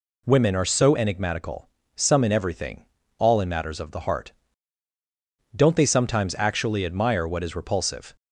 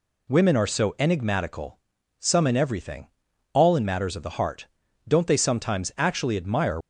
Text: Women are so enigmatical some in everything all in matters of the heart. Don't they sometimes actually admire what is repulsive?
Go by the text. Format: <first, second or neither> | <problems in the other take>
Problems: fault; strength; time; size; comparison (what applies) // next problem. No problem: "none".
first | pauses between "enigmatical" and "some"; at 1.7 s; 0.38 s long; slight in the first // pauses between "everything" and "all"; at 3.0 s; 0.44 s long; slight in the first // stops before "what is repulsive"; at 6.8 s